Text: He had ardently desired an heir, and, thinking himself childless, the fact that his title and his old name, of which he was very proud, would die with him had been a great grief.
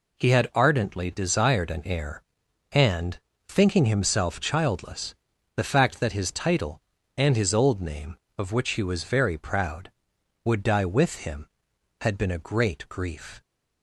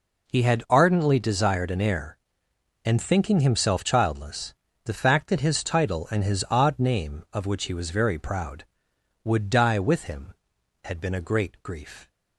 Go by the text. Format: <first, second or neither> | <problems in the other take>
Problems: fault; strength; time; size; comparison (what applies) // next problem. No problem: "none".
first | says "odd" for "old"; at 6.5 s